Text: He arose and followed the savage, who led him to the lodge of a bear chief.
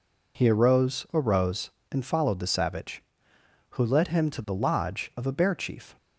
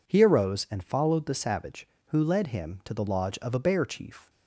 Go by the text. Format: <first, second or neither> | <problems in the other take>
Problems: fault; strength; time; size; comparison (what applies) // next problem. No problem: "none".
second | says "arose" twice; at 1.1 s